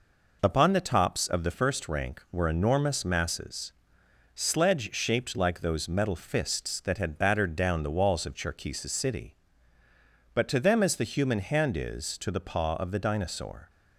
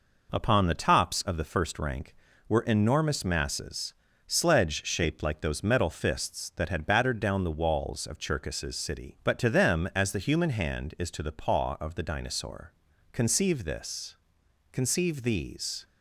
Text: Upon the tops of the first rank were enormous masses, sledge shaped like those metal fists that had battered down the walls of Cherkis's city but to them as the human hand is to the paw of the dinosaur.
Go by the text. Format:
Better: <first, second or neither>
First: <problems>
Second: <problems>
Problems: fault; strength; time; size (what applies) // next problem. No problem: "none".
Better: first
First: none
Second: goes on to say "Conceive this conceive these"; strong; from 13.1 s on; 2.7 s long